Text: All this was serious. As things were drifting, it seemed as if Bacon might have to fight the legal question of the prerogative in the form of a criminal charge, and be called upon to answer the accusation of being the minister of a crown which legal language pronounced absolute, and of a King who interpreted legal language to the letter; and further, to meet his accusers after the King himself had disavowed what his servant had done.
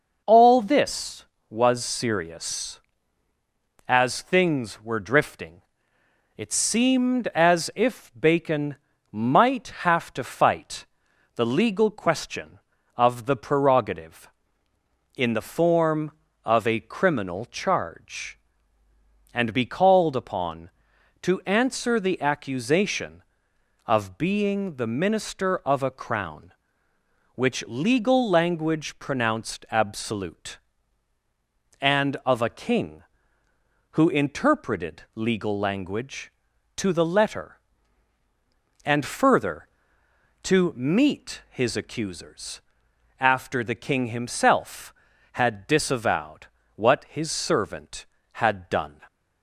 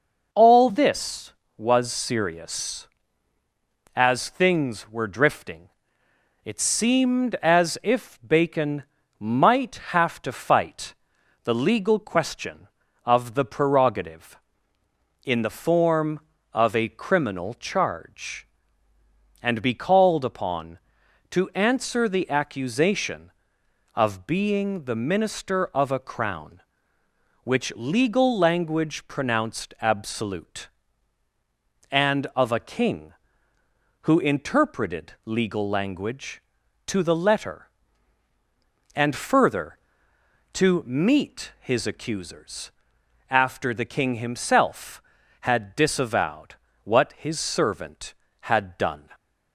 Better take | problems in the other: neither | pauses between "Bacon" and "might"; slight; the same in both // pauses between "fight" and "the"; noticeable; the same in both // pauses between "accusers" and "after"; noticeable; the same in both // pauses between "disavowed" and "what"; slight; the same in both

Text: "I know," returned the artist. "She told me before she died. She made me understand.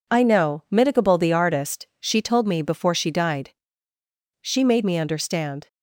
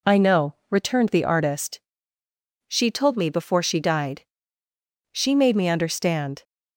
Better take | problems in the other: second | says "mitigable" for "returned"; at 0.6 s

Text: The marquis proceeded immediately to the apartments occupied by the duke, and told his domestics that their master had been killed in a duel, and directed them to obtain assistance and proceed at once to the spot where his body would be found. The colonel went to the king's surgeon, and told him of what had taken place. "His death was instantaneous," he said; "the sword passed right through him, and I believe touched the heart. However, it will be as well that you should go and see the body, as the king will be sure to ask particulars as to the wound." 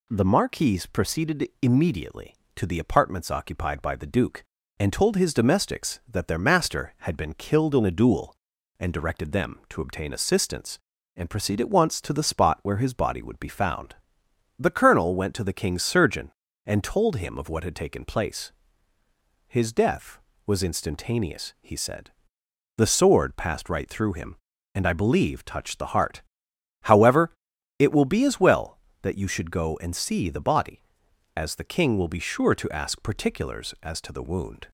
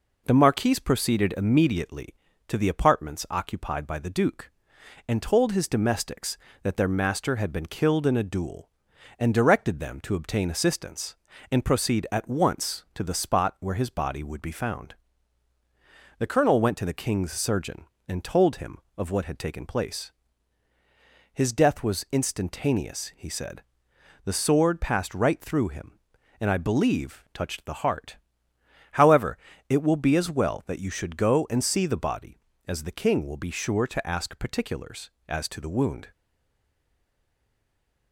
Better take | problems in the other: first | stays silent after the last word; noticeable; from 36.1 s on; 2.0 s long

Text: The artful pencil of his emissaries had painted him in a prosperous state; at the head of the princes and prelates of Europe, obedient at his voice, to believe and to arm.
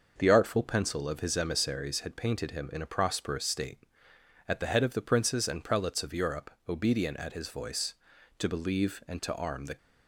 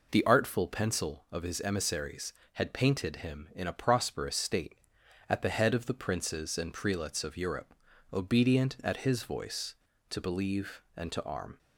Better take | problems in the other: second | goes on to say "The"; slight; from 9.6 s on; 0.10 s long

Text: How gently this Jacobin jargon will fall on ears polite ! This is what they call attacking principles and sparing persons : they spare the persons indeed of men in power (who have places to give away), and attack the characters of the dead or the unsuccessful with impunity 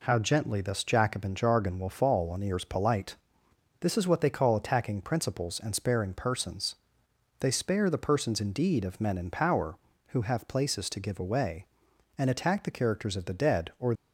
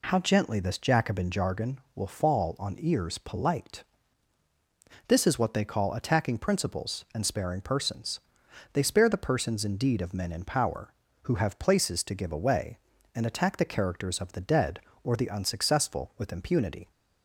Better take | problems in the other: second | stops before "the unsuccessful with impunity"; at 13.9 s

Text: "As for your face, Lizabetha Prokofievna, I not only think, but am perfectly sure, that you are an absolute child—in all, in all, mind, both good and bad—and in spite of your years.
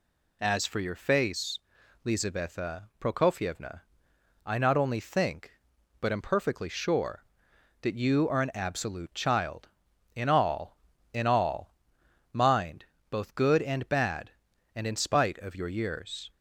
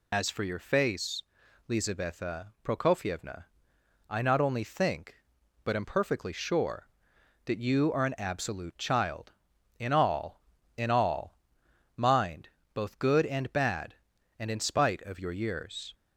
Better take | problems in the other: first | loses the start of "As"; at 0.1 s; 75 ms

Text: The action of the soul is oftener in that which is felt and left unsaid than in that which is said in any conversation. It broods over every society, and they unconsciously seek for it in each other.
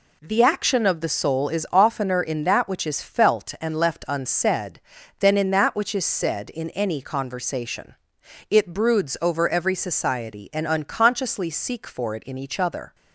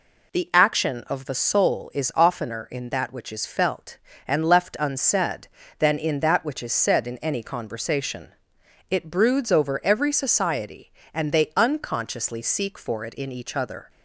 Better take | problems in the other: second | skips "they"; at 10.6 s

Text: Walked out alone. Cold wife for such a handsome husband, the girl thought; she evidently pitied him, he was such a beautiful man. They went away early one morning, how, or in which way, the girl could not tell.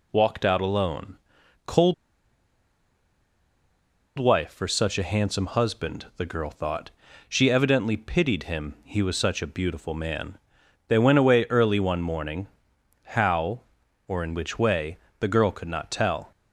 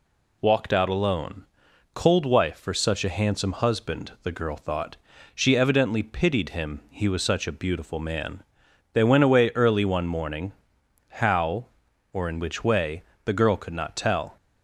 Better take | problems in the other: second | pauses between "Cold" and "wife"; strong; at 1.9 s; 2.2 s long

